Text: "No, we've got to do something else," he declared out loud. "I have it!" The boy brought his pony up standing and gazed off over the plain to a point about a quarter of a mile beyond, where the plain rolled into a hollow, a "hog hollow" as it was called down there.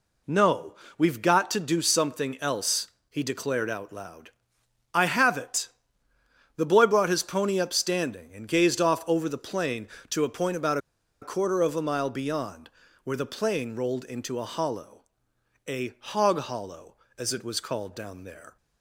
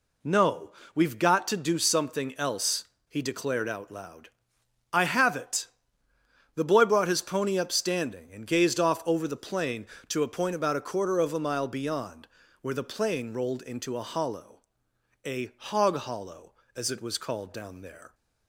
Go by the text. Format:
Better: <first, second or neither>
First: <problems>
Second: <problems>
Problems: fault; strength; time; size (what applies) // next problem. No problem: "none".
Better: second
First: pauses between "about" and "a"; at 10.7 s; 0.44 s long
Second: none